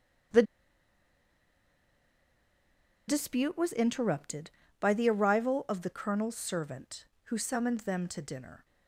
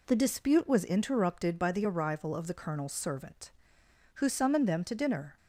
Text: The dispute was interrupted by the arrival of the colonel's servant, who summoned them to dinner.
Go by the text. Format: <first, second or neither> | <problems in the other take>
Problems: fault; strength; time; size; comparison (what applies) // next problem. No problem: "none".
second | starts louder than the rest; strong; until 3.9 s; 7.5 dB // pauses between "The" and "dispute"; strong; at 0.4 s; 2.6 s long